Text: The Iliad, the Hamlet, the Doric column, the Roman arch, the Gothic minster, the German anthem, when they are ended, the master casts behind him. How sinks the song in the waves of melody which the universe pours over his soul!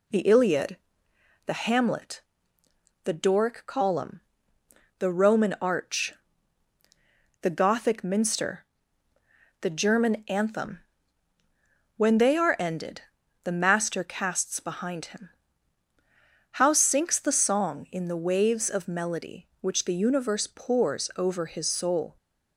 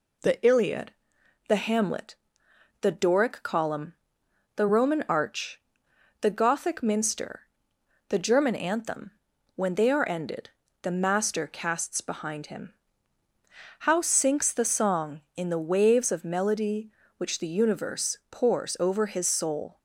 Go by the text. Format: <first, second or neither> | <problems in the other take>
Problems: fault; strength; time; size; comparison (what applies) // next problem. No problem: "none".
neither | none